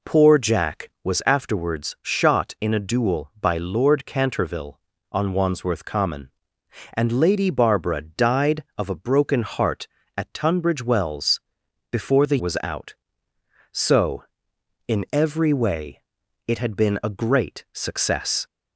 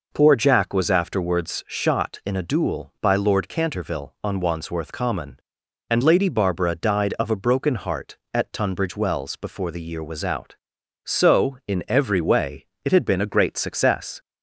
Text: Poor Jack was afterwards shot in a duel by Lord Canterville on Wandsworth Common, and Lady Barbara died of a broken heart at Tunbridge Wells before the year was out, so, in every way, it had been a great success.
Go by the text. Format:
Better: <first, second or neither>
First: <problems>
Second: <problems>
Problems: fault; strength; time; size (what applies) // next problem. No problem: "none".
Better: second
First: pauses between "Wells" and "before"; noticeable; at 11.3 s; 0.52 s long // skips "year"; at 12.3 s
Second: none